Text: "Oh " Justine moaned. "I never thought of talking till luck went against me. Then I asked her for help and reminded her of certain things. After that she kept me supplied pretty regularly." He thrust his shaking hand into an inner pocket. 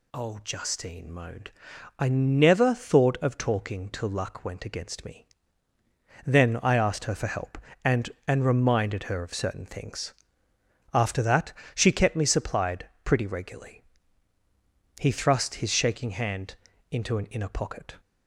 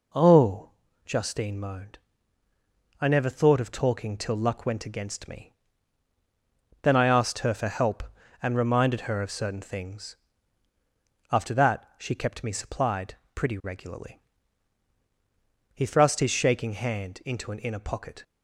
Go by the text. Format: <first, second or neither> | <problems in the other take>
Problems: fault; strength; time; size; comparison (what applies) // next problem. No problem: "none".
second | says "and" twice; at 8.2 s // pauses between "that" and "she"; slight; at 11.5 s; 0.24 s long // pauses between "supplied" and "pretty"; slight; at 12.8 s; 0.16 s long; slight in the second // pauses between "hand" and "into"; at 16.5 s; 0.38 s long